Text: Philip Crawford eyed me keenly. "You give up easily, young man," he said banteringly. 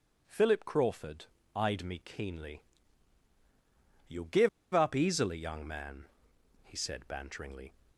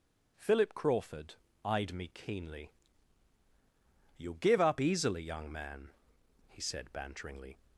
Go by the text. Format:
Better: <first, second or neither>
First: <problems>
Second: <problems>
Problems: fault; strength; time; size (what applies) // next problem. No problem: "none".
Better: second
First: pauses between "Crawford" and "eyed"; slight; at 1.2 s; 0.30 s long // pauses between "give" and "up"; slight; at 4.4 s; 0.24 s long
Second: pauses between "Crawford" and "eyed"; slight; at 1.3 s; 0.30 s long